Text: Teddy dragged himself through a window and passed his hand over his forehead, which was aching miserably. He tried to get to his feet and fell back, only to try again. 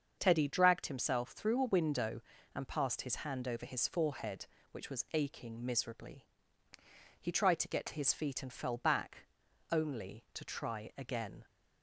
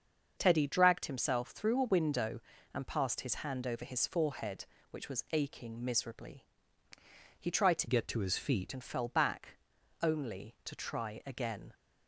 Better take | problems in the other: first | starts louder than the rest; until 1.3 s; 6.5 dB; also in the first // changes voice from "get" to "feet"; from 7.8 to 8.7 s; 0.9 s long

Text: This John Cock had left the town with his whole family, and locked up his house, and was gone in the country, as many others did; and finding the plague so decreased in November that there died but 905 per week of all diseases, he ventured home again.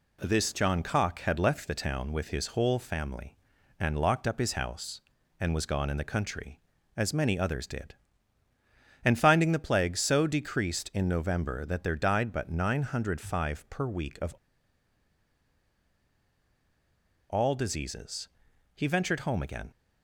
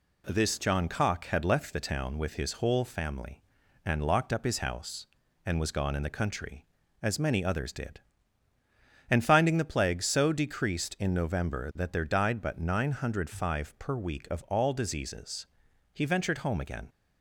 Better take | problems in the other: second | pauses between "of" and "all"; strong; at 14.3 s; 2.9 s long

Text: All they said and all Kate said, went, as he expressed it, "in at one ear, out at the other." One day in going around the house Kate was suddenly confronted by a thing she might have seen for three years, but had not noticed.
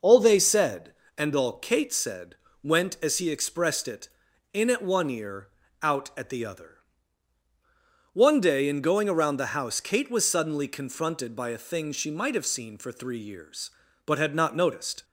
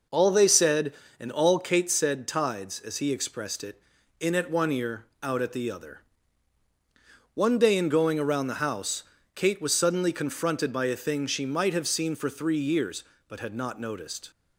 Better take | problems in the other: first | says "tides" for "went"; at 2.2 s // pauses between "house" and "Kate"; slight; at 9.0 s; 0.32 s long

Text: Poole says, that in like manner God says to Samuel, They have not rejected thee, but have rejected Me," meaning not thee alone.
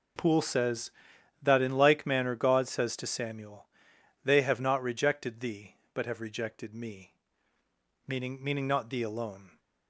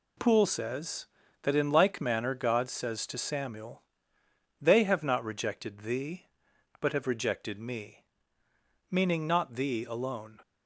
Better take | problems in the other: second | says "meaning" twice; at 8.4 s

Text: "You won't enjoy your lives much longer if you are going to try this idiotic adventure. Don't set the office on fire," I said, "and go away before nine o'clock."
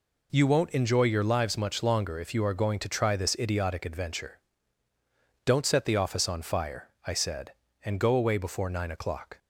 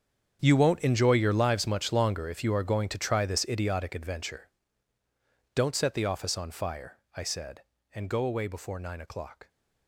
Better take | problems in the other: first | gets quieter; strong; throughout; 15 dB

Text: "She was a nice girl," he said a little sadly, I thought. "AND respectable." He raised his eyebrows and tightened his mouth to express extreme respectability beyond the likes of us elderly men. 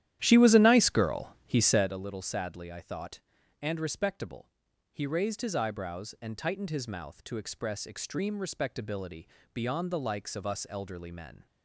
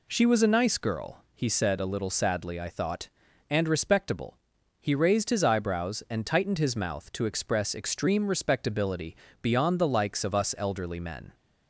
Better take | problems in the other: second | starts louder than the rest; strong; until 2.0 s; 12 dB // pauses between "respectability" and "beyond"; slight; at 9.2 s; 0.24 s long; slight in the second

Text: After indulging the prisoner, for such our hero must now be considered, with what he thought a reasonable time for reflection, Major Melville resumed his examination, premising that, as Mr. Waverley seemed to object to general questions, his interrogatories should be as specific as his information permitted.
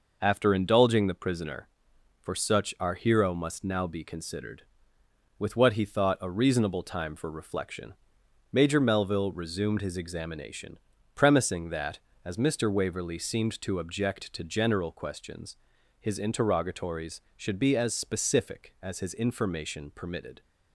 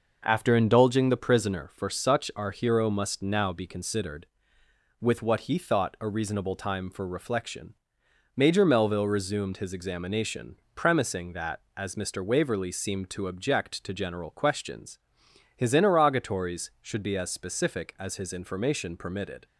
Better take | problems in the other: neither | none

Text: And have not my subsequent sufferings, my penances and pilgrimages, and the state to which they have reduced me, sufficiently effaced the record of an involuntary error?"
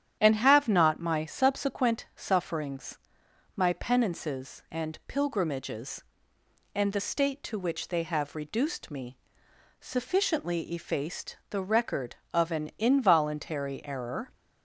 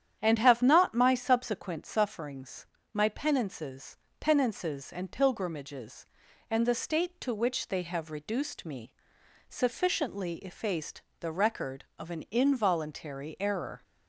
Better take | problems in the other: first | starts louder than the rest; strong; until 1.2 s; 9.5 dB; strong in the first // says "penances" twice; at 4.1 s // pauses between "effaced" and "the"; slight; at 11.0 s; 0.16 s long

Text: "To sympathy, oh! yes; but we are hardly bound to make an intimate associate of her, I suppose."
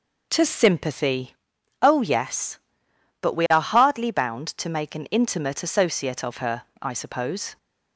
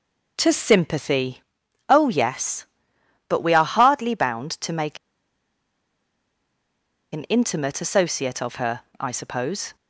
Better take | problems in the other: first | pauses between "make" and "an"; strong; at 4.9 s; 2.1 s long

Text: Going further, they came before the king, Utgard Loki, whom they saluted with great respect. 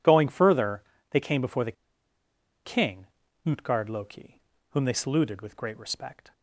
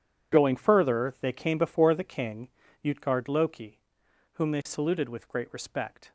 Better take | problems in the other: second | pauses between "the" and "king"; noticeable; at 1.7 s; 0.92 s long

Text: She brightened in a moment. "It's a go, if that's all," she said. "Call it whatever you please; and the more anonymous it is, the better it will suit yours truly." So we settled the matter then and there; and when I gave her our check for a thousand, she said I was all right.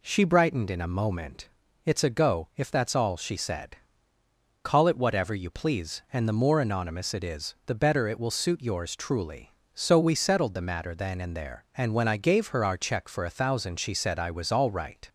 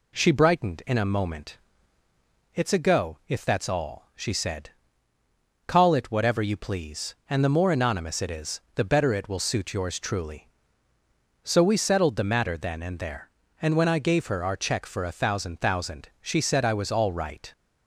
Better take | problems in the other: first | says "thousand" twice; at 15.6 s

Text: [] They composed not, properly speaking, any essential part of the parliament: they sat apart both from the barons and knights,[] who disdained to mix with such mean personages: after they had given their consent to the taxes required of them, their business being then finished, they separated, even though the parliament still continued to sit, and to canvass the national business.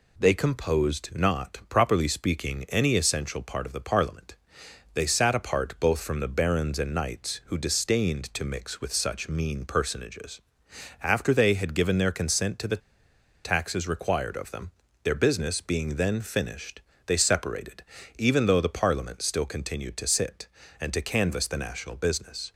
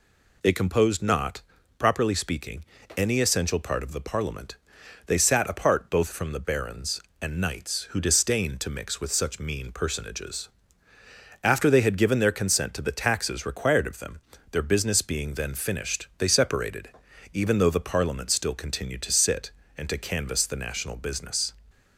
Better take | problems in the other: second | pauses between "the" and "taxes"; noticeable; at 12.8 s; 0.63 s long

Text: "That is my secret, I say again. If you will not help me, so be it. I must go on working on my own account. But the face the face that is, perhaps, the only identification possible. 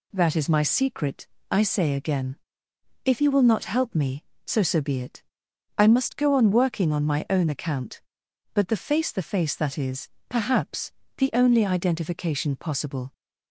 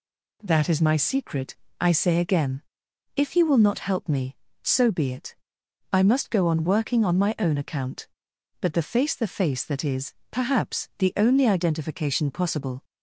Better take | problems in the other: second | says "so" twice; at 4.6 s

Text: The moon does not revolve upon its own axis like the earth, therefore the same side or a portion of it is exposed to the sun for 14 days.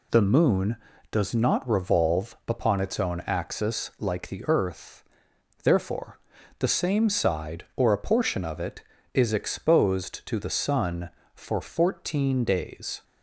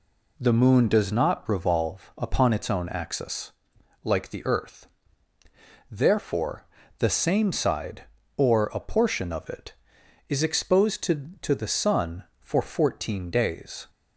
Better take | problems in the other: first | pauses between "axis" and "like"; noticeable; at 3.5 s; 0.52 s long // pauses between "therefore" and "the"; slight; at 6.6 s; 0.32 s long; also in the first // says "to" twice; at 11.3 s

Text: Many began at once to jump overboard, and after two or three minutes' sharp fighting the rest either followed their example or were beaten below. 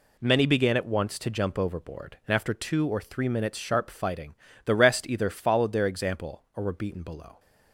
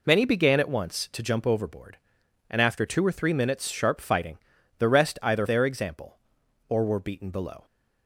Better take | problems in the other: first | pauses between "fighting" and "the"; at 4.3 s; 0.42 s long; slight in the first // skips "followed"; at 5.4 s

